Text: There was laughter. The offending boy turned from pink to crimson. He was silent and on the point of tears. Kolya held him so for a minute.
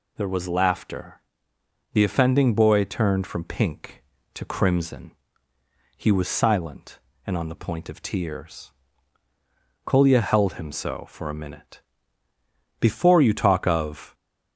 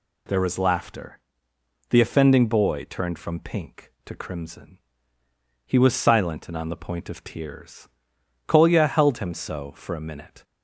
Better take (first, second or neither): second